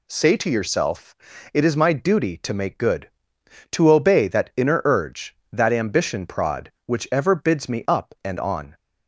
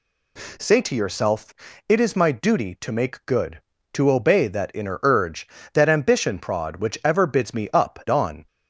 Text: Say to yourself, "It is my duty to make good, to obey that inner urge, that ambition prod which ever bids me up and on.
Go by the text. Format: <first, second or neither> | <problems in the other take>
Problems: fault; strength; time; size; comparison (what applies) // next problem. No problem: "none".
first | skips "and"; at 8.0 s